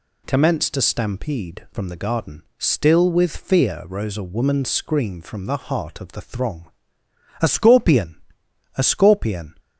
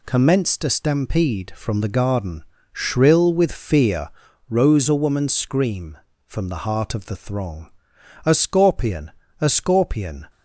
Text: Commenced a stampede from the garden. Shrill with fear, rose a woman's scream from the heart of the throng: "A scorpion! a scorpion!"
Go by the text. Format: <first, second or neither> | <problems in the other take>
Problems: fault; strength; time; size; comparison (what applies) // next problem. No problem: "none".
second | says "Still" for "Shrill"; at 2.5 s